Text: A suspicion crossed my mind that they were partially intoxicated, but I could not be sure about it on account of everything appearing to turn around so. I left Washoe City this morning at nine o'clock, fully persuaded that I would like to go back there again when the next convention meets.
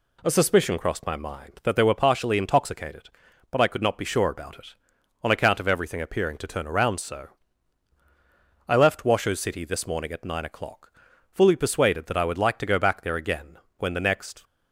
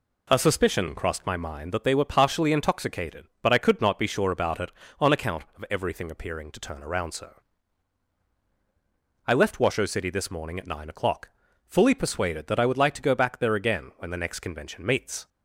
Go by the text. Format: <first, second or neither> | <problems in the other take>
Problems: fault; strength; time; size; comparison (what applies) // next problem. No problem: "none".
second | pauses between "again" and "when"; slight; at 13.5 s; 0.20 s long // stops before "convention meets"; at 14.4 s